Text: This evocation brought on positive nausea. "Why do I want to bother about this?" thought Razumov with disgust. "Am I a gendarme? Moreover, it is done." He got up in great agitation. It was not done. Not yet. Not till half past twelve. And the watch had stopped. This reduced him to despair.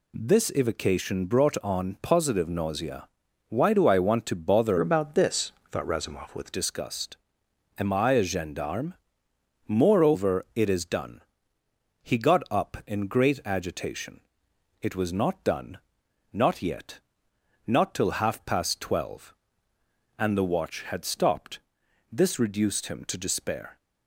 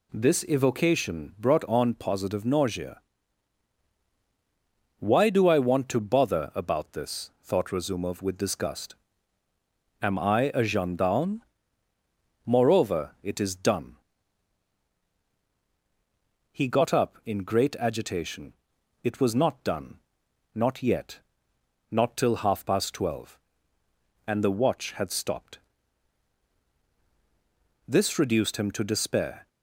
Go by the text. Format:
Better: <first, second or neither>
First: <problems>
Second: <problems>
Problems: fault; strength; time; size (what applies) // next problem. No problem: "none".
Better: second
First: changes voice from "about" to "with"; from 4.7 to 6.5 s; 1.8 s long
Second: none